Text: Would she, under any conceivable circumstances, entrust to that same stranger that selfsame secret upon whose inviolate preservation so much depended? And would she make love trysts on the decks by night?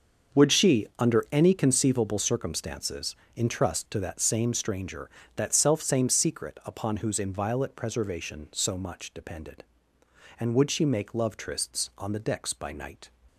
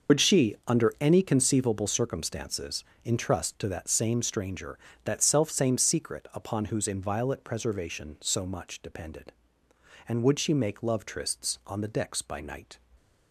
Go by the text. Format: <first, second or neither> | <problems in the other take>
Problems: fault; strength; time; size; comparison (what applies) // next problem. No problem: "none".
first | loses the start of "Would"; at 0.0 s; 75 ms // starts louder than the rest; noticeable; until 1.2 s; 6 dB; also in the first